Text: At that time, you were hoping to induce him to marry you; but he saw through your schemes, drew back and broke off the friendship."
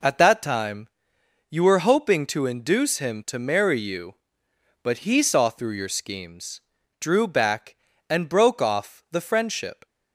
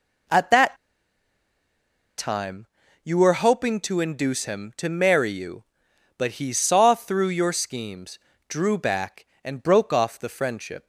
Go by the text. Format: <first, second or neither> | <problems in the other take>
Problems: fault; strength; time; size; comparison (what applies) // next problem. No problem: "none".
first | pauses between "that" and "time"; strong; at 0.7 s; 1.4 s long